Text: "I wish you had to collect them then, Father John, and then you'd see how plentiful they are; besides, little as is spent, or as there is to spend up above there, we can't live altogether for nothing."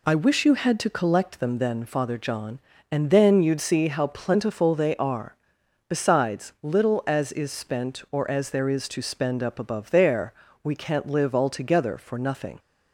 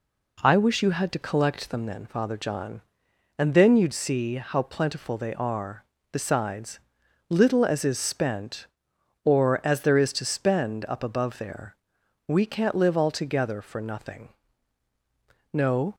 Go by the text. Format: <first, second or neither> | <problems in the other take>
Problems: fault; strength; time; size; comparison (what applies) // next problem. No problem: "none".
first | goes on to say "No"; slight; from 15.5 s on; 0.42 s long